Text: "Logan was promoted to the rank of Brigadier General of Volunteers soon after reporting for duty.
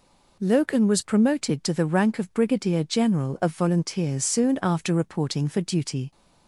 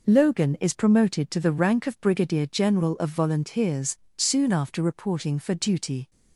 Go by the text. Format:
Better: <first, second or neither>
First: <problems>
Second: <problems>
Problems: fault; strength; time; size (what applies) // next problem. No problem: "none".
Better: first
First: none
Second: says "is" for "was"; at 0.5 s // pauses between "Volunteers" and "soon"; slight; at 3.9 s; 0.22 s long